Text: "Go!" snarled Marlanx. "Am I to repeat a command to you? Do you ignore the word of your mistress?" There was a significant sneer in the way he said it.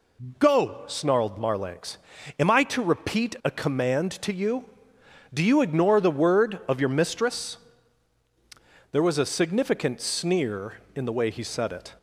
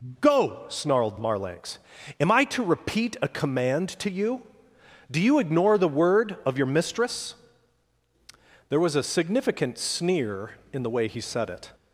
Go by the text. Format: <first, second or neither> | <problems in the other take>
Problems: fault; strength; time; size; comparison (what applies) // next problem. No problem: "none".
neither | none